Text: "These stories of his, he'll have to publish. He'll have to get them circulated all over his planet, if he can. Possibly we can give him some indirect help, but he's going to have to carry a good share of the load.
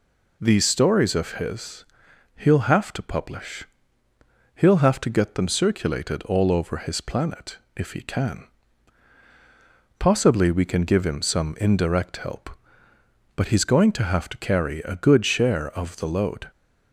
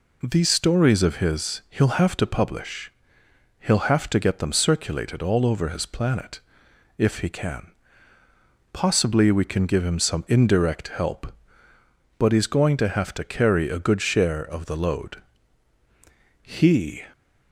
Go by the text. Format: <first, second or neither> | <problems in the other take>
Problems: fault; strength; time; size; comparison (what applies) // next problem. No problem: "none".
first | goes on to say "He"; from 16.4 s on; 0.60 s long